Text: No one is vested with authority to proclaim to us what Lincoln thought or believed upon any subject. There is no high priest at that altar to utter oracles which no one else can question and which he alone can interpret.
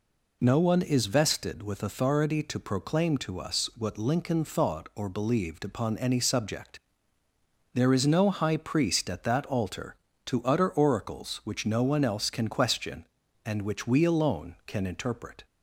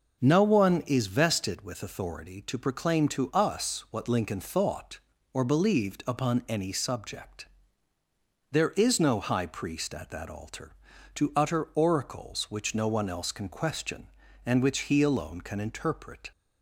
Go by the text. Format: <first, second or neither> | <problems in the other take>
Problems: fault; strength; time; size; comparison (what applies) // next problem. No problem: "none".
second | says "we" for "he"; at 13.8 s